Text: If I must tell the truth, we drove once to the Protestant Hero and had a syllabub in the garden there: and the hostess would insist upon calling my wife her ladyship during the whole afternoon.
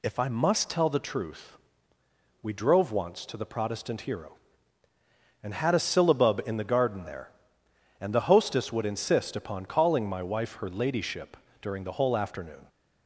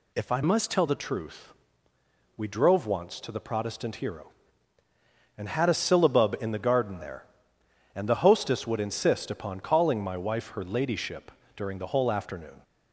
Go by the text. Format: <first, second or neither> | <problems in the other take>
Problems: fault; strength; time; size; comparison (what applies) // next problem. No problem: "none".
first | changes voice from "must" to "tell"; from 0.4 to 0.8 s; 0.4 s long // pauses between "ladyship" and "during"; slight; at 11.3 s; 0.24 s long; slight in the first